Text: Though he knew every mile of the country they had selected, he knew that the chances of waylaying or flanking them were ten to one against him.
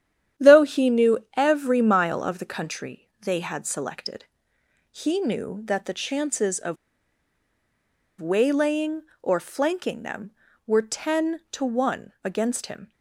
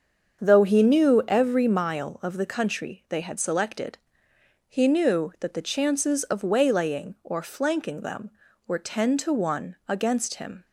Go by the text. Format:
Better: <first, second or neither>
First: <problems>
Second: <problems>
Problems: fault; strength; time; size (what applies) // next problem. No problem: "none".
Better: second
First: starts louder than the rest; strong; until 1.5 s; 10 dB // pauses between "of" and "waylaying"; strong; at 6.7 s; 1.4 s long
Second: starts louder than the rest; until 1.4 s; 7 dB